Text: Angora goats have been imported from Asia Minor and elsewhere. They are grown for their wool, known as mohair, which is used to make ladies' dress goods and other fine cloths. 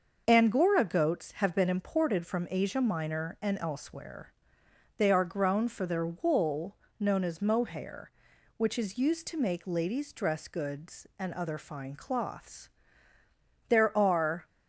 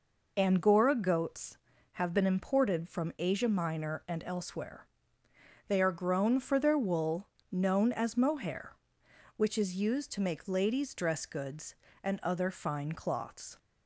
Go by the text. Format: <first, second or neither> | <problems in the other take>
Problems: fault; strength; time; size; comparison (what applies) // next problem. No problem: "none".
second | starts louder than the rest; noticeable; until 1.2 s; 6 dB // goes on to say "There are"; noticeable; from 13.6 s on; 0.78 s long